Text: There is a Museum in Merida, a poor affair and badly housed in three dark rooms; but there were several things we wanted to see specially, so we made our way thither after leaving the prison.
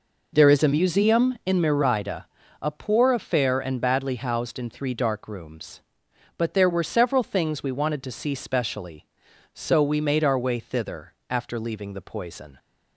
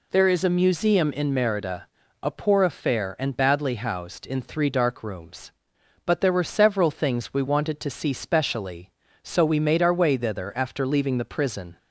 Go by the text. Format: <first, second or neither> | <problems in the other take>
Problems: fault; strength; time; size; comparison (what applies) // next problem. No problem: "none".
second | pauses between "thither" and "after"; slight; at 11.1 s; 0.16 s long // says "poison" for "prison"; at 12.0 s